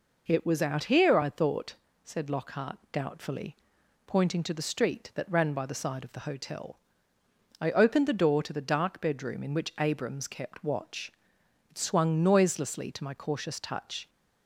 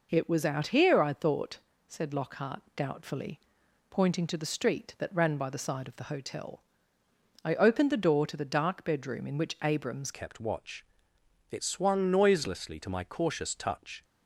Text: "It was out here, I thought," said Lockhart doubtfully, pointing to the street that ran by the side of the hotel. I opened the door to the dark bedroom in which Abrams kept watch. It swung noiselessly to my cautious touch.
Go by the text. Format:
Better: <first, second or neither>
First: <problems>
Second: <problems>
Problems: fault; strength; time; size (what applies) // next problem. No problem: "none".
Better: first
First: none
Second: changes voice at "kept"; from 10.1 s on; 3.9 s long